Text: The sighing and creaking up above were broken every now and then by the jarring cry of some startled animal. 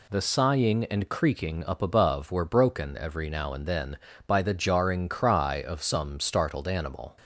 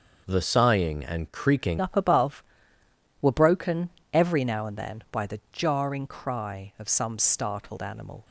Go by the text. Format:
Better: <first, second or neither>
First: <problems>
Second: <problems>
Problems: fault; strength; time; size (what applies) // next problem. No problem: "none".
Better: first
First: none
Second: starts louder than the rest; noticeable; until 1.2 s; 6 dB // changes voice at "up"; from 1.7 s on; 6.5 s long // pauses between "broken" and "every"; slight; at 3.8 s; 0.24 s long